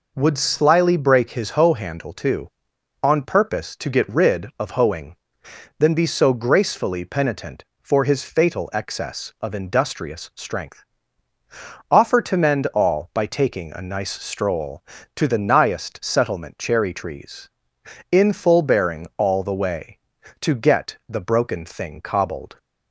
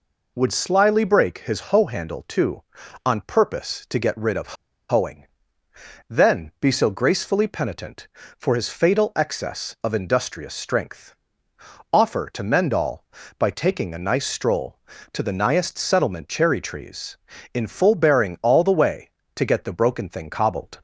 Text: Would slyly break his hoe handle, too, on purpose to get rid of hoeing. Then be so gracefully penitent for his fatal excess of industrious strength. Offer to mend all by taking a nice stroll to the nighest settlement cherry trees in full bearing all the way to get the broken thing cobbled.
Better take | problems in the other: first | pauses between "of" and "hoeing"; slight; at 4.5 s; 0.35 s long

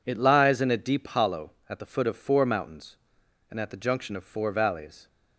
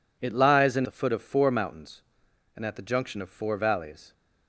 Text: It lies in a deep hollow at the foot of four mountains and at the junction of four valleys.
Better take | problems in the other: first | skips "a deep hollow at"; at 0.8 s

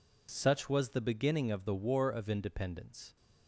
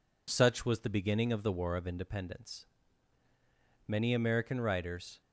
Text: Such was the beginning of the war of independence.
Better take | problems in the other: first | goes on to say "Many American writers"; from 3.8 s on; 1.3 s long

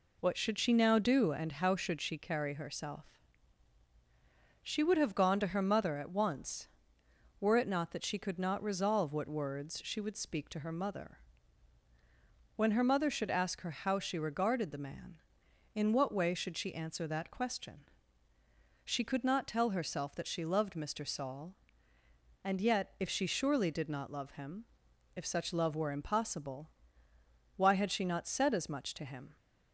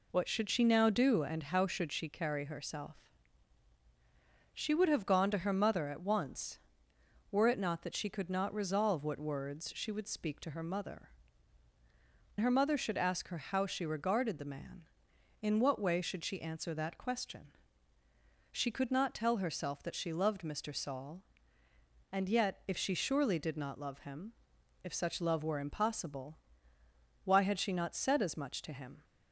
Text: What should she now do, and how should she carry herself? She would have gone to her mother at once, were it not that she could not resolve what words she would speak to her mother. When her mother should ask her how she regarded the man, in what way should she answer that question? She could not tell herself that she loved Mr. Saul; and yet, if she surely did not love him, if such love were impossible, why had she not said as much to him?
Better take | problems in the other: first | skips "When"; at 11.7 s

